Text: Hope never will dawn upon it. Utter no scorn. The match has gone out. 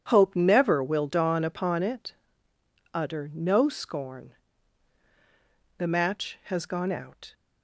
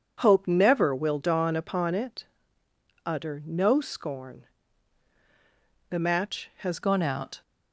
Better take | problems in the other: first | changes voice at "gone"; from 6.8 s on; 0.6 s long

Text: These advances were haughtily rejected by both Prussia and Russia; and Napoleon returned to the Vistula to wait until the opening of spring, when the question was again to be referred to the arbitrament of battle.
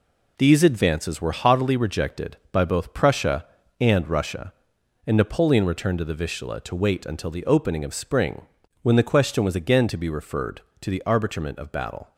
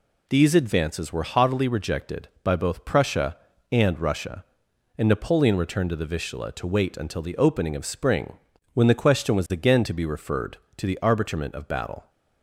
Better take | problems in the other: second | gets quieter; strong; throughout; 7 dB

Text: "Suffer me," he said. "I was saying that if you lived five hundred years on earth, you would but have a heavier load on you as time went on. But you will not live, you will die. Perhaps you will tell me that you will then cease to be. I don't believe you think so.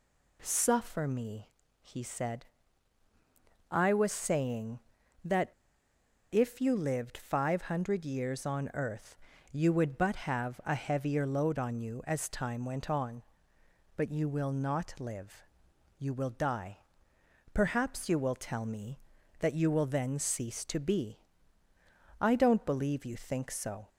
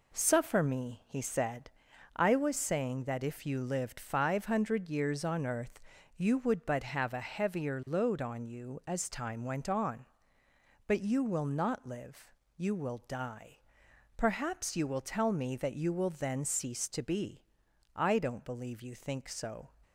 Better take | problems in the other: second | pauses between "that" and "if"; noticeable; at 5.5 s; 0.80 s long

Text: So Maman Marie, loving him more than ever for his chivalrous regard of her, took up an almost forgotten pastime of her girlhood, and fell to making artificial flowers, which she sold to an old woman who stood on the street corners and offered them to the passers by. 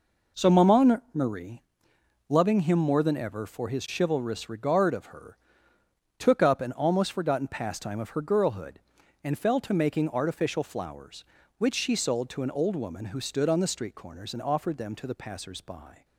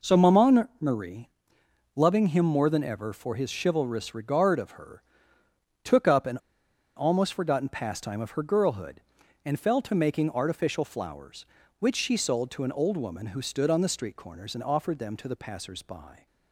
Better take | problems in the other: first | pauses between "an" and "almost"; noticeable; at 6.3 s; 0.58 s long

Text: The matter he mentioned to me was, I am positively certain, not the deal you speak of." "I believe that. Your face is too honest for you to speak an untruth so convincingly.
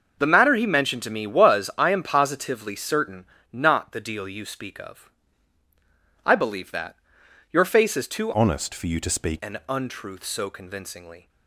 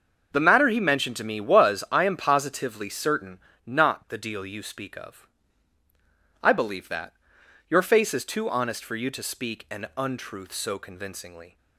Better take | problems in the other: second | starts louder than the rest; noticeable; until 1.2 s; 6 dB; also in the second // changes voice from "honest" to "speak"; from 8.3 to 9.3 s; 1.0 s long

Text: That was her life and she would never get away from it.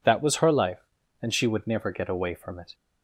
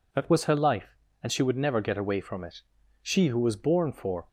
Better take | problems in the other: first | goes on to say "She who was born for"; noticeable; from 3.0 s on; 1.2 s long

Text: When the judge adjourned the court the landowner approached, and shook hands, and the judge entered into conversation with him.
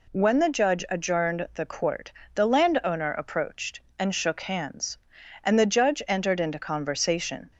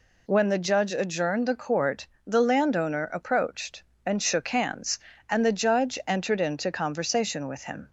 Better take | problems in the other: second | pauses between "court" and "the"; slight; at 2.1 s; 0.20 s long; slight in the second // stops before "with him"; at 7.5 s

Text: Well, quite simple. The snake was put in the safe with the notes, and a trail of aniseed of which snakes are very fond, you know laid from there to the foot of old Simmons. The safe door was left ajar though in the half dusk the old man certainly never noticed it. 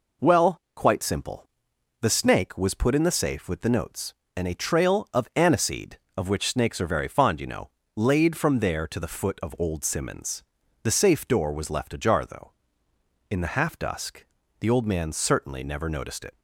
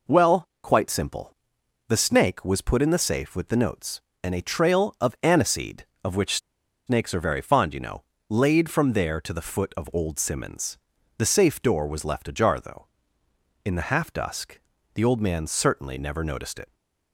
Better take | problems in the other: first | pauses between "which" and "snakes"; noticeable; at 6.3 s; 0.49 s long // pauses between "know" and "laid"; slight; at 8.0 s; 0.26 s long; slight in the first // pauses between "dusk" and "the"; slight; at 14.5 s; 0.34 s long; slight in the first

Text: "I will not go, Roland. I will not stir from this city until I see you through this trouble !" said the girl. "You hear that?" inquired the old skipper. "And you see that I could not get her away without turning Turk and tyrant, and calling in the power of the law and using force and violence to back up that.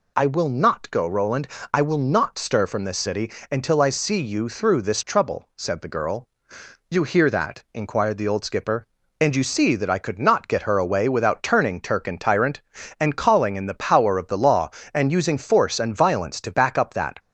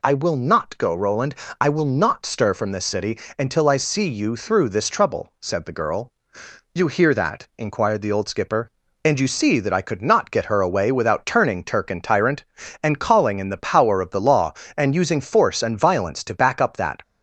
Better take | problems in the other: neither | pauses between "city" and "until"; slight; the same in both

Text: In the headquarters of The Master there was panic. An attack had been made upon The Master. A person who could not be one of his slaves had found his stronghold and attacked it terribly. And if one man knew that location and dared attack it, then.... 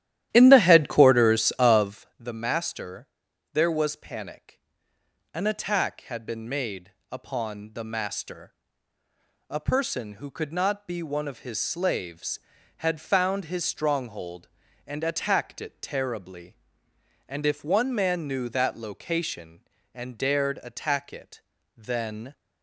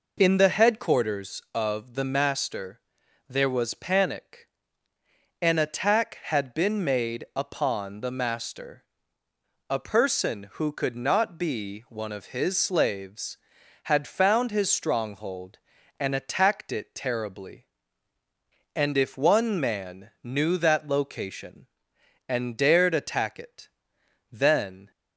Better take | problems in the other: second | starts louder than the rest; strong; until 2.0 s; 12.5 dB // pauses between "Master" and "there"; at 3.0 s; 0.44 s long; noticeable in the second // pauses between "made" and "upon"; slight; at 6.9 s; 0.18 s long

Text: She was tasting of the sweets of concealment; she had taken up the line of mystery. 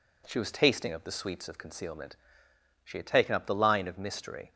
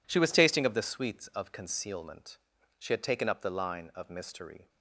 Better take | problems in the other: neither | none

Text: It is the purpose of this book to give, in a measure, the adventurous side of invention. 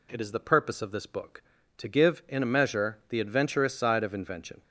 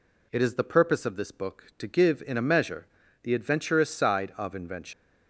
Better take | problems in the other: first | leaves "invention" unfinished; at 4.9 s; 150 ms

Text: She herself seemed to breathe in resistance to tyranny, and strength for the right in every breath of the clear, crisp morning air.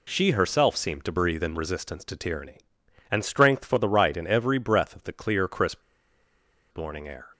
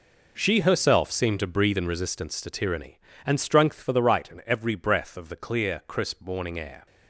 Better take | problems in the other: second | pauses between "crisp" and "morning"; noticeable; at 5.7 s; 0.94 s long

